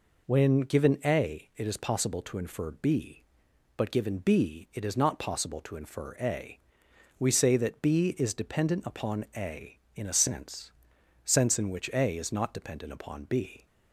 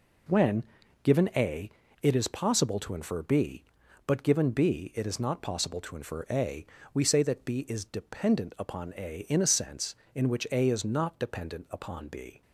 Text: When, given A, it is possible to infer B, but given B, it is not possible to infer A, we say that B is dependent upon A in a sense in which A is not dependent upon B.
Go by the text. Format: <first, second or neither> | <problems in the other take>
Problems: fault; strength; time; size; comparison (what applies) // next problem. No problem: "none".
second | says "sense" twice; at 11.2 s